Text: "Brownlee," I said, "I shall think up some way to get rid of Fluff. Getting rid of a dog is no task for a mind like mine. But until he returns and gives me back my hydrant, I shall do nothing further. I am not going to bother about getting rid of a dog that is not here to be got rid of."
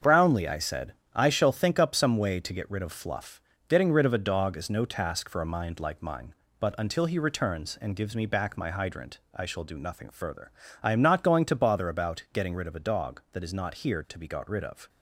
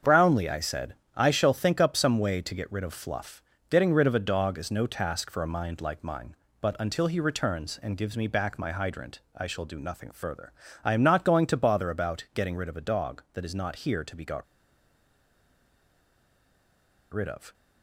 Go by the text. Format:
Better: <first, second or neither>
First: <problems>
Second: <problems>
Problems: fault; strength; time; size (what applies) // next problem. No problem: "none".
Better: first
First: starts louder than the rest; until 1.2 s; 7 dB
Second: starts louder than the rest; until 1.2 s; 7 dB // pauses between "got" and "rid"; strong; at 14.4 s; 2.6 s long